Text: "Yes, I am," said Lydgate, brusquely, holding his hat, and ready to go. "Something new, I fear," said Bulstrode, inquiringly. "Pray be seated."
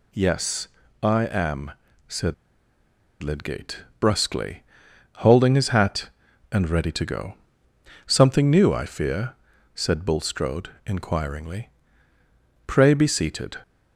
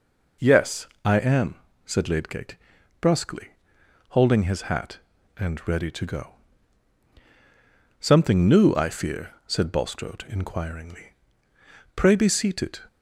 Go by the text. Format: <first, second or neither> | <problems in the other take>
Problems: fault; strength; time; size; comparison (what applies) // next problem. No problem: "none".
second | pauses between "said" and "Lydgate"; noticeable; at 2.3 s; 0.88 s long